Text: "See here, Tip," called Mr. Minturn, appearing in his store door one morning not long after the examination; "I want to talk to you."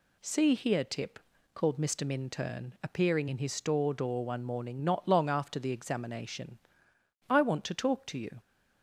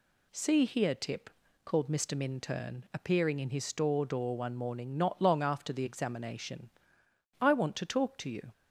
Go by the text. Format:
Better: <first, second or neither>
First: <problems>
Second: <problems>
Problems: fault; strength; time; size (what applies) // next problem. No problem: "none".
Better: neither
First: none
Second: none